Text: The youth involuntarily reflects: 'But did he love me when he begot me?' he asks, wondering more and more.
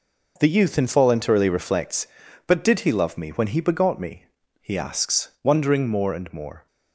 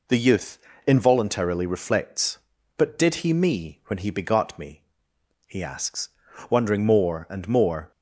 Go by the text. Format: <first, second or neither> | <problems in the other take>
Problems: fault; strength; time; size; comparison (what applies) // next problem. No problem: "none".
first | pauses between "youth" and "involuntarily"; slight; at 0.5 s; 0.26 s long // skips "love"; at 3.3 s